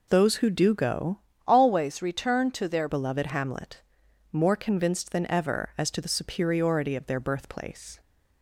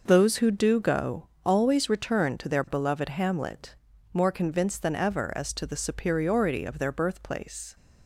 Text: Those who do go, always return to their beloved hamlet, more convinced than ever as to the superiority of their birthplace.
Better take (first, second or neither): second